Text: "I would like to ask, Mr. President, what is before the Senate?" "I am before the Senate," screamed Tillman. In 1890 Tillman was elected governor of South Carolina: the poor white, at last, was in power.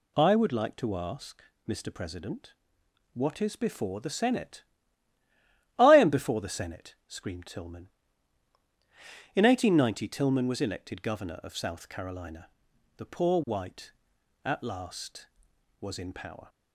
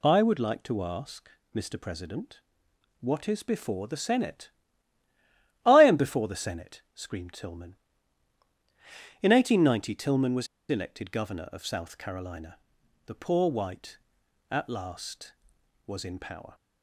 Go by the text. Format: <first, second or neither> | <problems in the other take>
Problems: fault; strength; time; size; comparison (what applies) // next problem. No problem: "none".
first | pauses between "was" and "elected"; slight; at 10.4 s; 0.24 s long